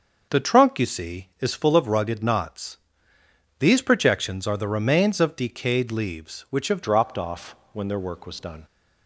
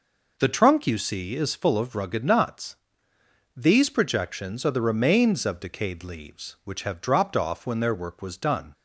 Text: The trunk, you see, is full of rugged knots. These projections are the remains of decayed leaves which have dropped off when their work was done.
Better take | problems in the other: second | starts louder than the rest; noticeable; until 1.4 s; 6 dB // changes voice at "dropped"; from 6.8 s on; 1.8 s long // pauses between "off" and "when"; slight; at 7.5 s; 0.18 s long

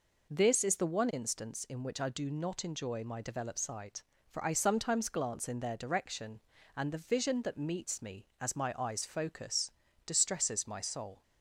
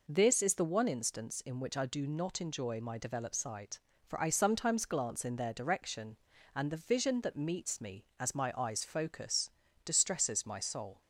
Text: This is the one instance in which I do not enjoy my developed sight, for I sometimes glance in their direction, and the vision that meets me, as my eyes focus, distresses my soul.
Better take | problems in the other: neither | none

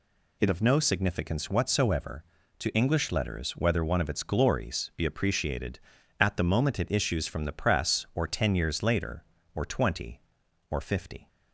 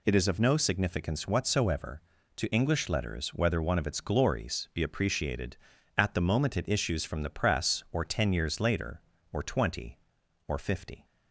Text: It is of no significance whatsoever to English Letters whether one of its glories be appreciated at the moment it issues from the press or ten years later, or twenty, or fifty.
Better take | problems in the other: second | skips "is"; at 0.4 s

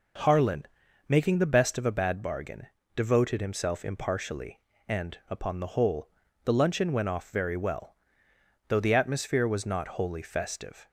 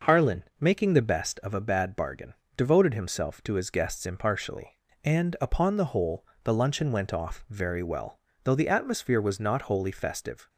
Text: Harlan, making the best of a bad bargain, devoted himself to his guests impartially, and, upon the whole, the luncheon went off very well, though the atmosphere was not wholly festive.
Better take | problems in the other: second | skips "to his guests"; at 3.8 s

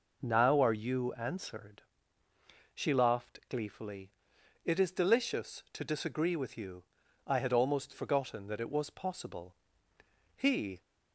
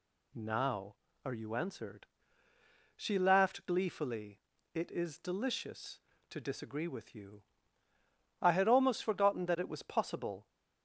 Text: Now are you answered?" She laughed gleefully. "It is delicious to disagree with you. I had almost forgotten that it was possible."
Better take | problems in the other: second | goes on to say "He"; slight; from 10.3 s on; 0.46 s long

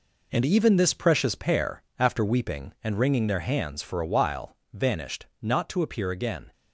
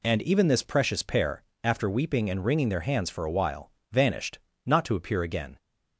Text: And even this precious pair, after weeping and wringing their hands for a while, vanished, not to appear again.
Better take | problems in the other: second | gets quieter; strong; throughout; 8.5 dB

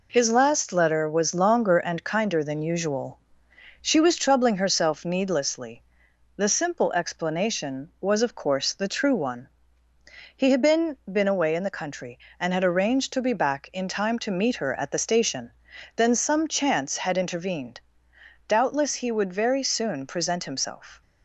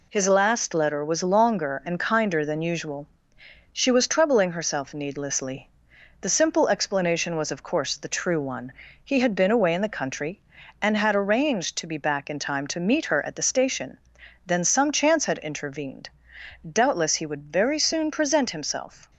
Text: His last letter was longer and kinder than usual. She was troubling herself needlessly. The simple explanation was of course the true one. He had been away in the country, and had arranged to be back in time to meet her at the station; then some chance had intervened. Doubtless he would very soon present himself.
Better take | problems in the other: second | says "been" twice; at 11.1 s

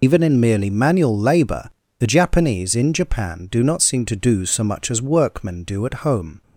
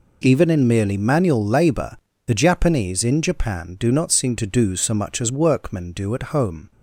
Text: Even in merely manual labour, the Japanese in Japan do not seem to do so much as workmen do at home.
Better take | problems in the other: second | loses the start of "Even"; at 0.0 s; 85 ms

